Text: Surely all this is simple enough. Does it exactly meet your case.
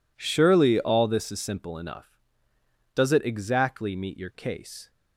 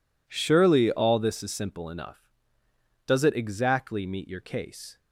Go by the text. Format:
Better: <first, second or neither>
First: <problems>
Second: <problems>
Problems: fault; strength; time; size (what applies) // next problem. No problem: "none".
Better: neither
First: none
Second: none